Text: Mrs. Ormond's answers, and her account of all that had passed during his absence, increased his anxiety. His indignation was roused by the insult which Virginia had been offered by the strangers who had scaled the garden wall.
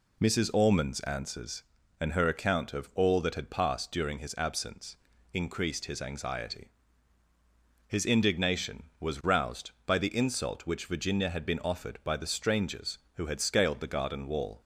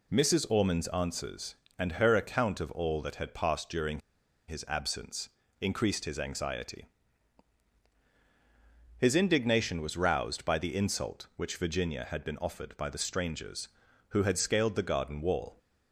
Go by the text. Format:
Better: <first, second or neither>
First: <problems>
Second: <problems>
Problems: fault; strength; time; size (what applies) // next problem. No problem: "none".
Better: first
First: none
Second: pauses between "during" and "his"; noticeable; at 3.9 s; 0.49 s long